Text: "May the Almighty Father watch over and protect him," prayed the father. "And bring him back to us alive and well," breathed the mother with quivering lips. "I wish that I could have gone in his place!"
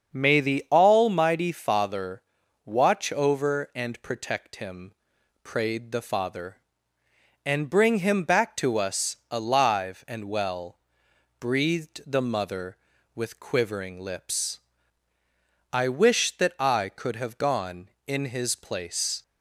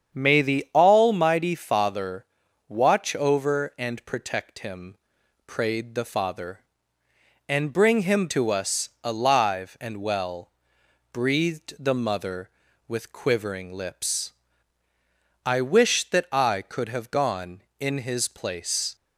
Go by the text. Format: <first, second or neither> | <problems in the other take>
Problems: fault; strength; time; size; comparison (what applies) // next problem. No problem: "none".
first | starts louder than the rest; strong; until 1.2 s; 8 dB; also in the first // pauses between "Father" and "watch"; at 2.2 s; 0.42 s long; also in the first // skips "back"; at 8.2 s